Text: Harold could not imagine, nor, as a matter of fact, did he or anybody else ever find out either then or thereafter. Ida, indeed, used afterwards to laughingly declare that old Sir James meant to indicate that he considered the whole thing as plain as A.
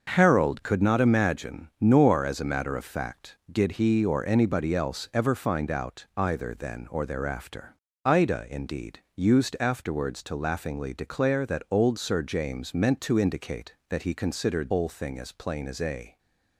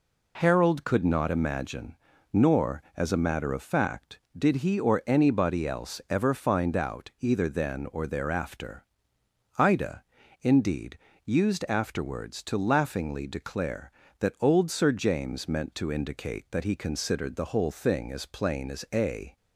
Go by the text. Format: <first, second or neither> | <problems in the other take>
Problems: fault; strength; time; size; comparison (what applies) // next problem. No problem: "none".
second | starts louder than the rest; until 1.1 s; 6.5 dB // skips "the"; at 14.7 s